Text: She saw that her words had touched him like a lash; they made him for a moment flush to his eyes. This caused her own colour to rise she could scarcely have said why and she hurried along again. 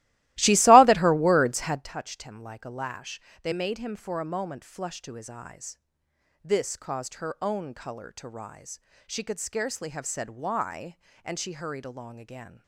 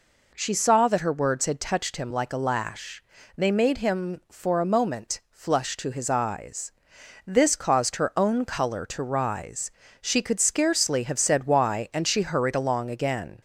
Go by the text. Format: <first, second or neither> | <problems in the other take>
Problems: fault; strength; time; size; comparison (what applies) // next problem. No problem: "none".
second | starts louder than the rest; strong; until 1.9 s; 17.5 dB // pauses between "rise" and "she"; slight; at 8.7 s; 0.30 s long; slight in the second